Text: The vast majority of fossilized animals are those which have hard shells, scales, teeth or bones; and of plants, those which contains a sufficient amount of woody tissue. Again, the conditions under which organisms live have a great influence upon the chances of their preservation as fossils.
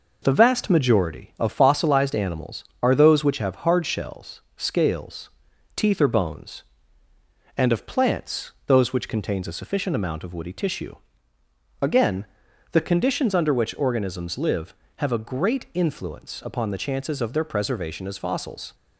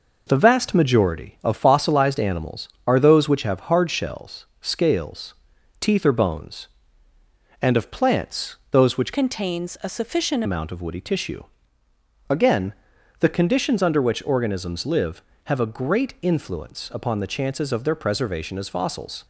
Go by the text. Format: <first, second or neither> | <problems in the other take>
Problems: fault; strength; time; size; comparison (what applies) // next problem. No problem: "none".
first | changes voice from "contains" to "sufficient"; from 9.1 to 10.4 s; 1.3 s long